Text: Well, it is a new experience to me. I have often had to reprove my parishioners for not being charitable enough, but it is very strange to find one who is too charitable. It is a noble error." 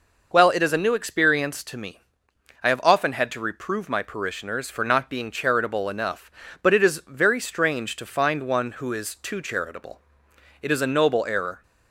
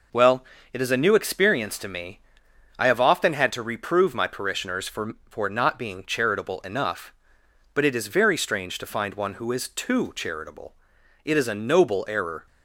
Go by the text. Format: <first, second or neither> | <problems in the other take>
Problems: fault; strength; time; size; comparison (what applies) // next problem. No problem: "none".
first | says "for" twice; at 5.2 s